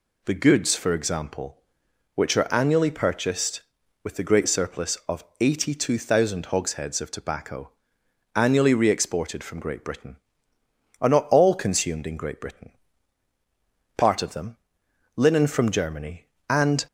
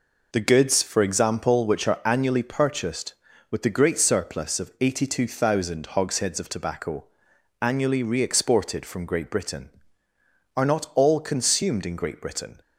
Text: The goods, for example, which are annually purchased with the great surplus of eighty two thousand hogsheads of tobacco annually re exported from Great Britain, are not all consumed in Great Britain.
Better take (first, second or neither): second